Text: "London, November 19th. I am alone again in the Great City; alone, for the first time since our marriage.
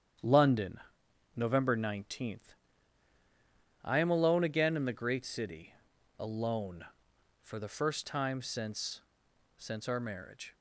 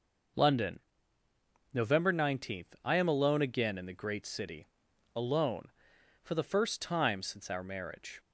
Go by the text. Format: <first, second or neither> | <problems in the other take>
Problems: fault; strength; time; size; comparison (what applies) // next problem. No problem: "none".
second | starts louder than the rest; strong; until 1.7 s; 9 dB // says "since" twice; at 9.5 s